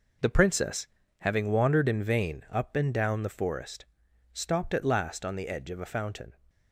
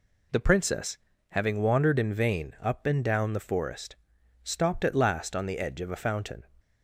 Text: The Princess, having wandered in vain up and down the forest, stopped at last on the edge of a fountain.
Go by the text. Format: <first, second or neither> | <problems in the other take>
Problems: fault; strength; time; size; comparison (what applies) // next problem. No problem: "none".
second | gets quieter; strong; throughout; 9 dB